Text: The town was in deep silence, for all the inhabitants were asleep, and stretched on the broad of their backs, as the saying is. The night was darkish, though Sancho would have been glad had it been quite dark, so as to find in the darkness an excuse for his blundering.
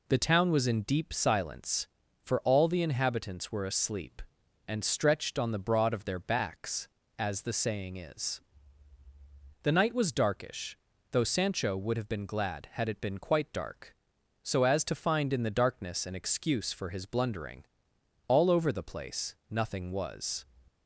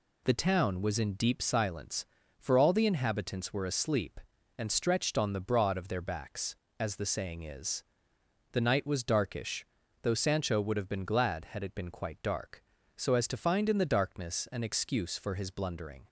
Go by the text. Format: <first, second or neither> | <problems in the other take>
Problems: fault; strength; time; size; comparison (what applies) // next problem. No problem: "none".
second | goes on to say "All over the place nothing was"; strong; from 18.2 s on; 2.1 s long